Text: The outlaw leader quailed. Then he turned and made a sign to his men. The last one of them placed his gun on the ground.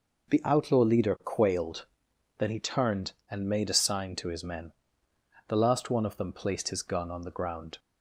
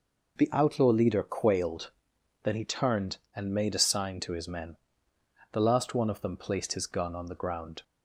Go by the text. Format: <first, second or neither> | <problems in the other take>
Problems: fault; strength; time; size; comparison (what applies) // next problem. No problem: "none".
neither | none